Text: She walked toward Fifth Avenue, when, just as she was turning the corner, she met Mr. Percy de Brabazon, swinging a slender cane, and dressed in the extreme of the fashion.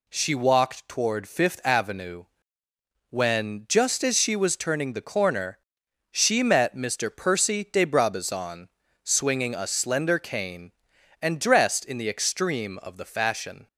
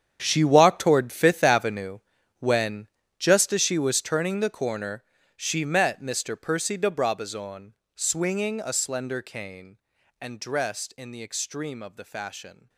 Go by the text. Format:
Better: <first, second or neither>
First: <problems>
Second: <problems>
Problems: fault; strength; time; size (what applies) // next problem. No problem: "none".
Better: first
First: none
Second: gets quieter; strong; throughout; 16 dB